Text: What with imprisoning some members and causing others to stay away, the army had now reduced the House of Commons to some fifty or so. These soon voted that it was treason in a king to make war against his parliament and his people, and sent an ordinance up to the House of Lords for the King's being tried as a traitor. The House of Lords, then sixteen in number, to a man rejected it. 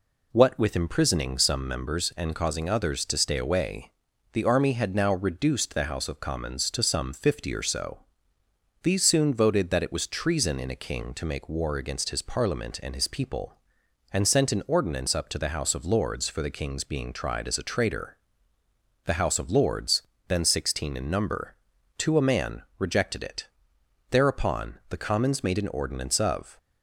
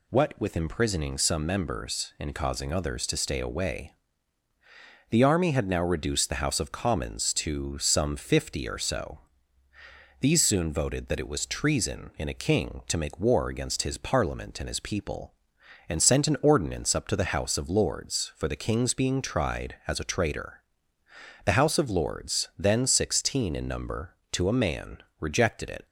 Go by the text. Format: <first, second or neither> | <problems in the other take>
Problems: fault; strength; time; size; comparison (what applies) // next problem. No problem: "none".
second | pauses between "man" and "rejected"; slight; at 22.6 s; 0.16 s long; slight in the second // goes on to say "Thereupon the Commons made an ordinance of"; strong; from 24.1 s on; 2.4 s long